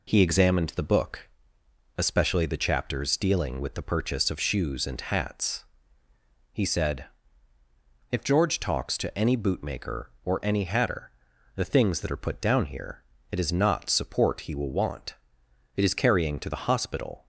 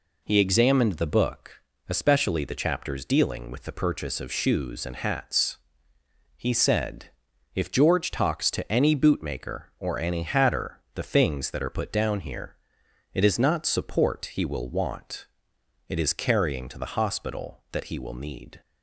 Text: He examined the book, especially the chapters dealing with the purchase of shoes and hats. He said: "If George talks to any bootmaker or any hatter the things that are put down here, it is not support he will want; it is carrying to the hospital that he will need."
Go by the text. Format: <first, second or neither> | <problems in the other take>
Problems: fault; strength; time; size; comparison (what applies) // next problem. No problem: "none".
second | pauses between "hatter" and "the"; noticeable; at 11.1 s; 0.46 s long; slight in the second // stops before "that he will need"; at 17.2 s